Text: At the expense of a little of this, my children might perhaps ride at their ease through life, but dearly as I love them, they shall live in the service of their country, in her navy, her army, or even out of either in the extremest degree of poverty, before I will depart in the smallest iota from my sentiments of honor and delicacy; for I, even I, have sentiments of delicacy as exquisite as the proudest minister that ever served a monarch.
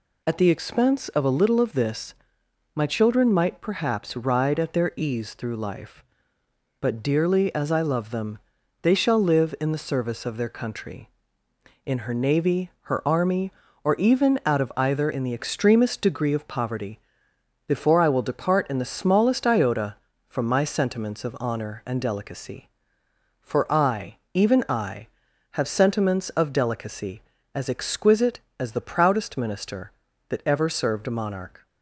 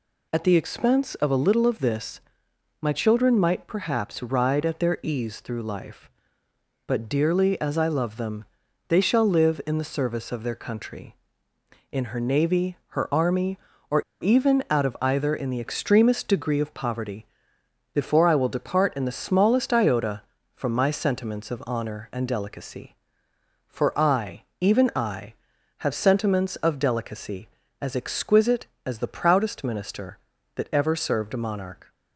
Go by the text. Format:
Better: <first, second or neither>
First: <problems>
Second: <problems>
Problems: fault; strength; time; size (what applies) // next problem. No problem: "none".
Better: first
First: none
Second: pauses between "or" and "even"; slight; at 14.0 s; 0.18 s long